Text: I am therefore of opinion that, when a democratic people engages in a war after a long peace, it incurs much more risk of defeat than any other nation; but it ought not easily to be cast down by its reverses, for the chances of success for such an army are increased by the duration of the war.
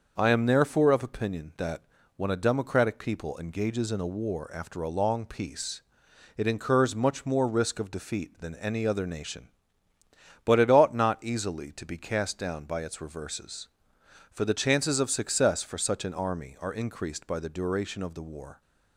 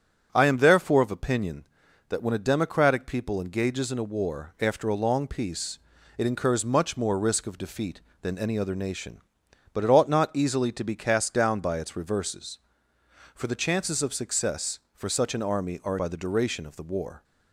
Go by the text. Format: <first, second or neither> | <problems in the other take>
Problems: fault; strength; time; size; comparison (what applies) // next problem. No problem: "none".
first | starts louder than the rest; strong; until 1.3 s; 7.5 dB; also in the first // skips "increased"; at 15.9 s